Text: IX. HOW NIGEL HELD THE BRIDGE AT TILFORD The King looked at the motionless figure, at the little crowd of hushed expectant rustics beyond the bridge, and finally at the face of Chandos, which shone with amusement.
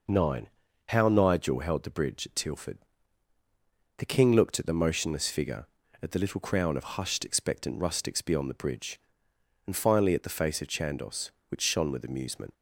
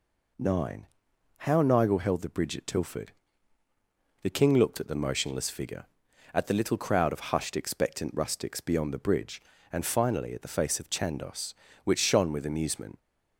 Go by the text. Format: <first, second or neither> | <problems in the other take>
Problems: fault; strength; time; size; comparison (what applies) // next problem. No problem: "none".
second | pauses between "TILFORD" and "The"; at 2.7 s; 1.2 s long; also in the second // says "crown" for "crowd"; at 6.4 s